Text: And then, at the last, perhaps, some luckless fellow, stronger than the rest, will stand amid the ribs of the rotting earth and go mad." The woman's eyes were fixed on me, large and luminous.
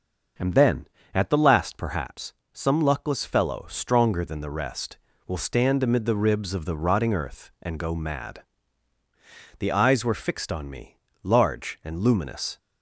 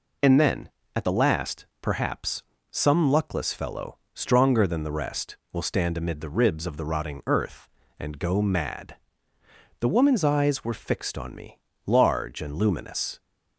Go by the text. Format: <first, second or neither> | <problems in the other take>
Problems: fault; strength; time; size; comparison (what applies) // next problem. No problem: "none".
second | starts louder than the rest; noticeable; until 1.6 s; 6 dB // skips "woman's"; at 9.7 s